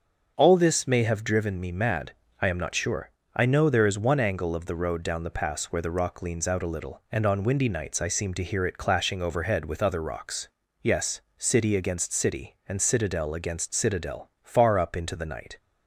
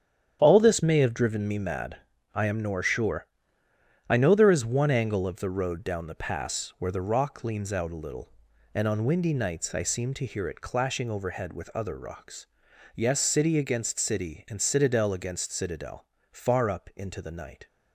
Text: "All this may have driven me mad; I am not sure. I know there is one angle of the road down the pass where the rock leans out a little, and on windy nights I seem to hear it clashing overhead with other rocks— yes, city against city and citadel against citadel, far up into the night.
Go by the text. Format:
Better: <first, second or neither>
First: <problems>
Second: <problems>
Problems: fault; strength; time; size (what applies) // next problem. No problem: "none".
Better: first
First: starts louder than the rest; until 1.3 s; 6.5 dB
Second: starts louder than the rest; strong; until 1.4 s; 9 dB // says "nor" for "not"; at 2.6 s